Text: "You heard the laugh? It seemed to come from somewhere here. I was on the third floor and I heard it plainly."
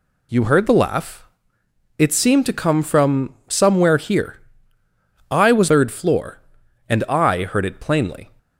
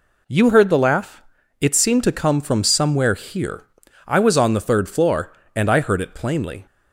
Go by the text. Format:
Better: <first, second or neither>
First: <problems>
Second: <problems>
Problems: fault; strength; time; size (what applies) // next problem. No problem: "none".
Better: second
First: skips "on the"; at 5.6 s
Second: none